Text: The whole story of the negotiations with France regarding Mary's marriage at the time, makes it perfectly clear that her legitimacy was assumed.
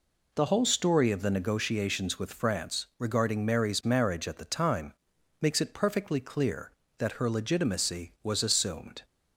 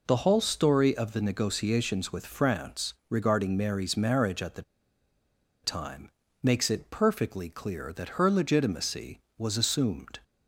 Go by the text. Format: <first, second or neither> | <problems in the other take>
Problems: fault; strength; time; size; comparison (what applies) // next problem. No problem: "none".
first | pauses between "France" and "regarding"; slight; at 2.9 s; 0.16 s long // pauses between "the" and "time"; at 4.6 s; 1.0 s long